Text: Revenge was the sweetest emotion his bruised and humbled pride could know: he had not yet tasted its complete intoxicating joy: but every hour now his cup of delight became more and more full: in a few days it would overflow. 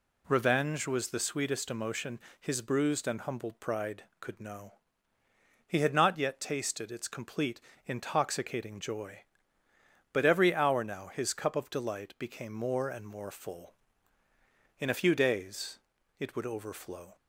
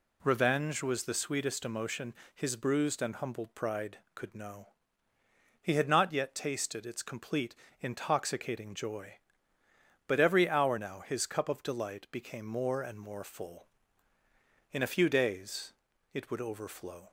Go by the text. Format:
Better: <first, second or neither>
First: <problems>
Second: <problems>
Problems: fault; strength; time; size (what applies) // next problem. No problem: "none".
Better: neither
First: pauses between "emotion" and "his"; slight; at 2.1 s; 0.22 s long // pauses between "complete" and "intoxicating"; slight; at 7.5 s; 0.26 s long // pauses between "days" and "it"; at 15.7 s; 0.40 s long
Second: pauses between "emotion" and "his"; slight; at 2.1 s; 0.22 s long // pauses between "complete" and "intoxicating"; slight; at 7.5 s; 0.26 s long // pauses between "days" and "it"; at 15.7 s; 0.40 s long